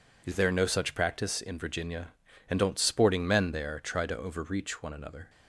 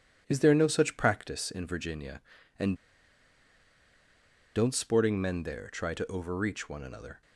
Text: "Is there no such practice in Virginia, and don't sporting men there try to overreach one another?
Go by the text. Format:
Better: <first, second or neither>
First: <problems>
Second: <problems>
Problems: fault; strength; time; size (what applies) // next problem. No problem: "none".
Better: first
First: none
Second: pauses between "and" and "don't"; strong; at 2.7 s; 1.8 s long